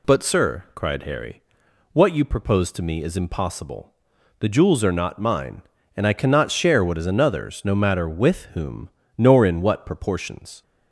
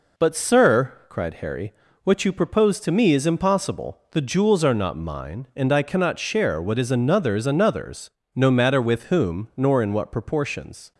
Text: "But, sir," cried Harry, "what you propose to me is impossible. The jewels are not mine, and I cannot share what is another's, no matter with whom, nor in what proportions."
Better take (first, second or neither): first